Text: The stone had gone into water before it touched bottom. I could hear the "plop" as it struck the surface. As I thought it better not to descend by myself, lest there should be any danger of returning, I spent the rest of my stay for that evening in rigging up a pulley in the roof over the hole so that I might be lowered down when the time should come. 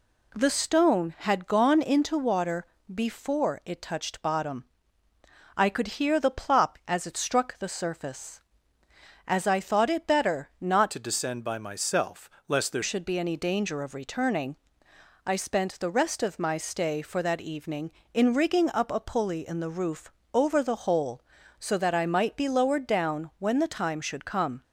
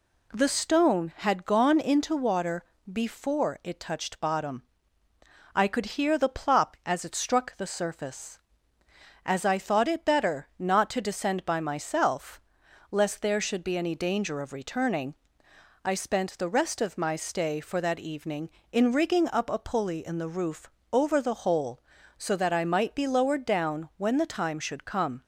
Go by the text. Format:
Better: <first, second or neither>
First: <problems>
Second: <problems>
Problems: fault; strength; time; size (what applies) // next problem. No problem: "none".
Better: second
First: pauses between "water" and "before"; slight; at 2.6 s; 0.26 s long // changes voice from "to" to "there"; from 10.9 to 12.8 s; 1.9 s long // pauses between "roof" and "over"; slight; at 20.1 s; 0.22 s long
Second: pauses between "water" and "before"; slight; at 2.6 s; 0.26 s long // pauses between "roof" and "over"; slight; at 20.6 s; 0.22 s long